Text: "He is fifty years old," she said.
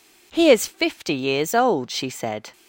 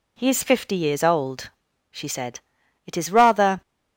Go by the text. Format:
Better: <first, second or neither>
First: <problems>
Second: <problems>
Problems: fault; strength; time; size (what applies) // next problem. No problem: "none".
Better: first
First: none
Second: goes on to say "It is rather"; noticeable; from 2.8 s on; 0.74 s long